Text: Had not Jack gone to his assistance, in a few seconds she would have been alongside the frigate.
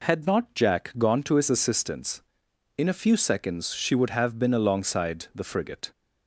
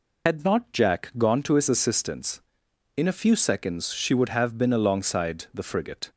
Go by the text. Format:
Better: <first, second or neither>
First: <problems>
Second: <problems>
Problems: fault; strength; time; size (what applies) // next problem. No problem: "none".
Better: first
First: none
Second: loses the start of "Had"; at 0.2 s; 80 ms